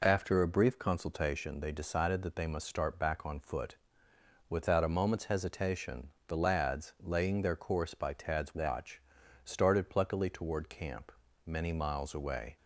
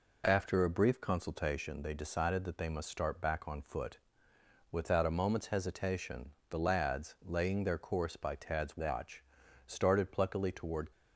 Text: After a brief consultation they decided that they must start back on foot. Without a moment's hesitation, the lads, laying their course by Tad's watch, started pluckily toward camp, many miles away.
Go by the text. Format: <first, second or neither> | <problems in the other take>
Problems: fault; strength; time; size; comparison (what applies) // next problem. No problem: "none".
first | stops before "camp many miles away"; at 10.9 s